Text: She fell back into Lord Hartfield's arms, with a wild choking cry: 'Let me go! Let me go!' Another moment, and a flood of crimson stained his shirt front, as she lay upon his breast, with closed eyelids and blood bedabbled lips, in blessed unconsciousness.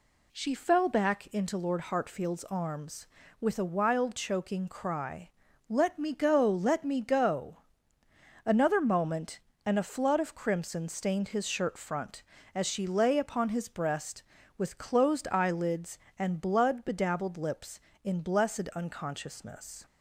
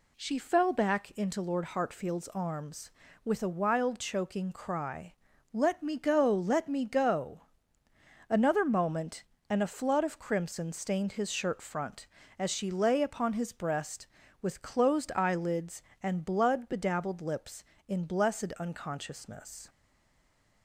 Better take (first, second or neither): first